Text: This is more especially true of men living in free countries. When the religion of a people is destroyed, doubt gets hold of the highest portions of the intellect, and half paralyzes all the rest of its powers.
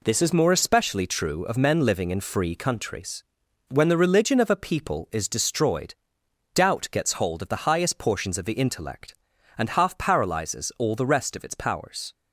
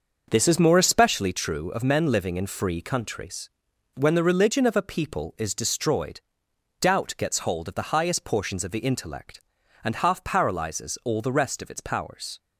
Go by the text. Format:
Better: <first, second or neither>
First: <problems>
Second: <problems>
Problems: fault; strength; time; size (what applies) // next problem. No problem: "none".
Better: first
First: none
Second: starts louder than the rest; until 1.4 s; 6 dB